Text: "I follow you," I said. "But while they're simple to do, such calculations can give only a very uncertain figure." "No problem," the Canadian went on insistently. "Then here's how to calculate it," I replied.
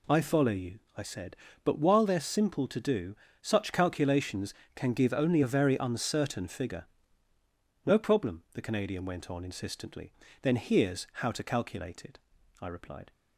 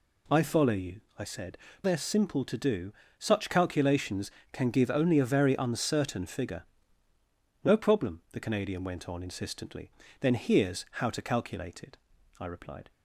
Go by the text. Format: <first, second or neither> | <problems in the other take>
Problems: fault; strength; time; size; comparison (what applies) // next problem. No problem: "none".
first | skips "But while"; at 1.7 s